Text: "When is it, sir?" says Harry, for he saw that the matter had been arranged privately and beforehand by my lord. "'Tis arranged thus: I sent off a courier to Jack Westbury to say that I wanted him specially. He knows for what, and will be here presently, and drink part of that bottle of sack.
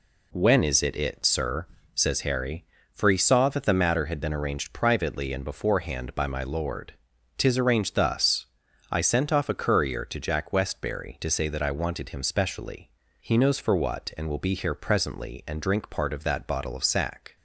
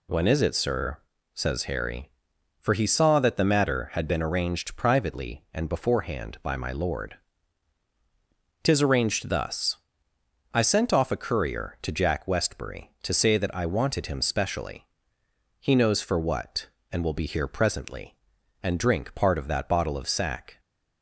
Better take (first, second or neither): second